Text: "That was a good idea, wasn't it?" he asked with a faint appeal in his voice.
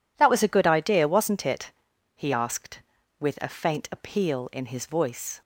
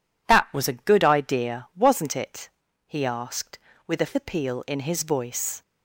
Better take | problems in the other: first | skips "faint"; at 4.1 s

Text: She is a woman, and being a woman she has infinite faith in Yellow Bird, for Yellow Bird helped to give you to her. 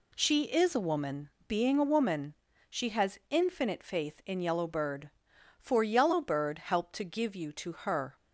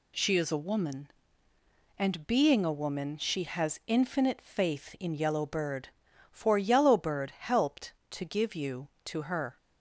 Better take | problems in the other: second | skips "and"; at 1.3 s // pauses between "woman" and "she"; slight; at 2.3 s; 0.34 s long

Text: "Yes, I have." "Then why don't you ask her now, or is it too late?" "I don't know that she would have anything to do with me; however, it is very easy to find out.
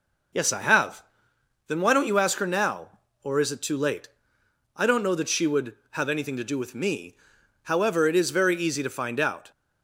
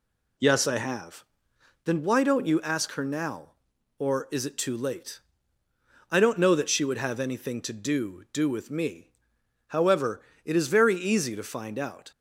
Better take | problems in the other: first | says "do" twice; at 8.3 s

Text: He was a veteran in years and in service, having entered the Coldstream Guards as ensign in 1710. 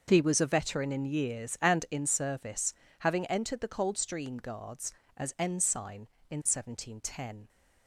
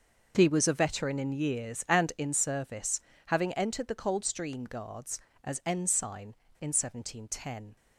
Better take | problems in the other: neither | starts louder than the rest; noticeable; the same in both

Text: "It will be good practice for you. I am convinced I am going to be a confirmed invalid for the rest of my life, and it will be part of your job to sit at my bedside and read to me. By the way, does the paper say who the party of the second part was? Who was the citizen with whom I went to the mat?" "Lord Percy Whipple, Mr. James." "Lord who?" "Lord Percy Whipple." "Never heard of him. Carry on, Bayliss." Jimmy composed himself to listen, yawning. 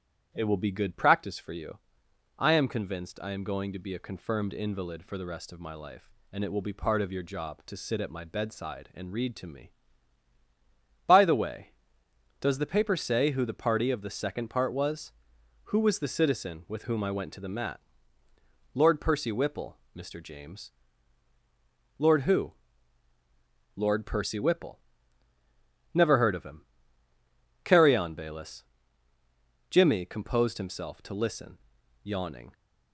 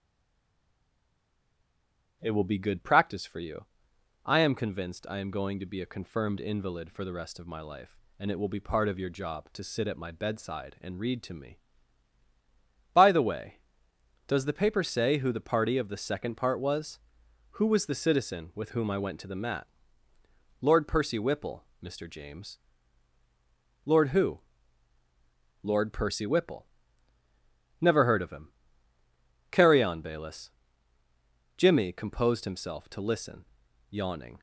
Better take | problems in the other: first | stays silent before the first word; until 2.1 s; 2.1 s long // starts louder than the rest; strong; until 3.2 s; 10 dB; strong in the first

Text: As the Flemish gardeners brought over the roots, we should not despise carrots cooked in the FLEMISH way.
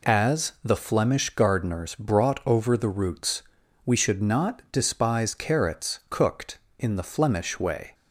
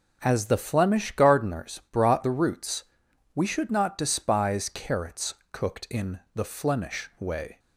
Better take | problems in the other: first | skips "over"; at 2.2 s // pauses between "carrots" and "cooked"; slight; at 5.3 s; 0.16 s long

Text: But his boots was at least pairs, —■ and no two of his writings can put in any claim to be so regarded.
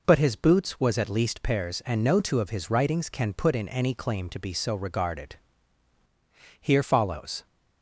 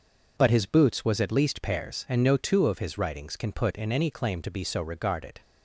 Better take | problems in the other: second | goes on to say "Here follows"; noticeable; from 6.5 s on; 0.86 s long

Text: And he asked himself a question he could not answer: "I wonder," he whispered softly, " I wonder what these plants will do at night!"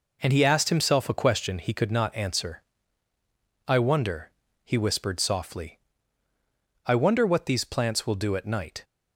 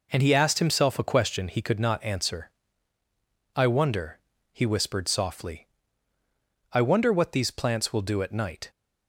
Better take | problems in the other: neither | none

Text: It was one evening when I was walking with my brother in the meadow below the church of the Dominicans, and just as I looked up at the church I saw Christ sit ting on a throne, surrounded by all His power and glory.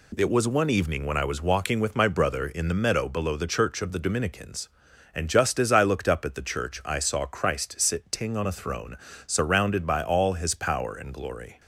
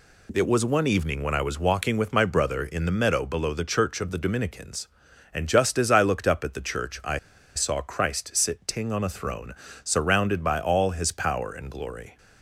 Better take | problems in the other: first | pauses between "I" and "saw"; at 7.1 s; 0.37 s long

